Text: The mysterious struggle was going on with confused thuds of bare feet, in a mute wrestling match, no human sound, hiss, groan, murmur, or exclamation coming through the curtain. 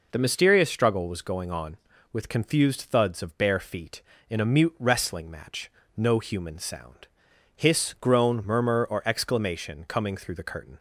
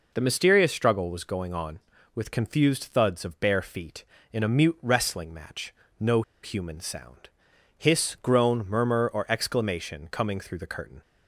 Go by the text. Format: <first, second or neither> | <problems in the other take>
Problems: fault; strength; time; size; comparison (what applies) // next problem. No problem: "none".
first | pauses between "no" and "human"; slight; at 6.2 s; 0.20 s long